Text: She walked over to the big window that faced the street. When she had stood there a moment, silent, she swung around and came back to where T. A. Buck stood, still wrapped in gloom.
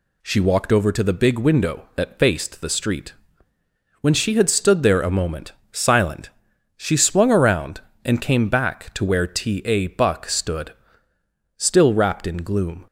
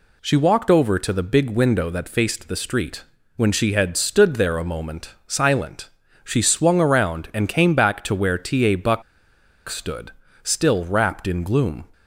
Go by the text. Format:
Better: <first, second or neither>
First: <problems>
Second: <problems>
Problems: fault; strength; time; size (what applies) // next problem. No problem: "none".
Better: first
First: none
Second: pauses between "Buck" and "stood"; noticeable; at 9.0 s; 0.66 s long